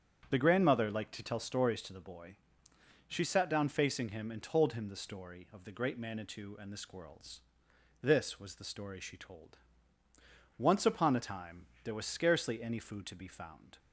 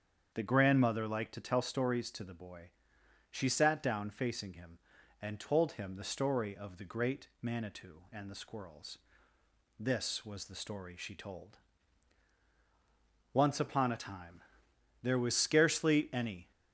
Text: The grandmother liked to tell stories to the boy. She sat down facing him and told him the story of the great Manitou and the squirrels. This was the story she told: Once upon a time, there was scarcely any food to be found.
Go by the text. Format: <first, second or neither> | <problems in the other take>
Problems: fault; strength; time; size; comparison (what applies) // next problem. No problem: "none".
first | starts louder than the rest; strong; until 1.3 s; 7.5 dB; also in the first // stops before "food to be found"; at 16.5 s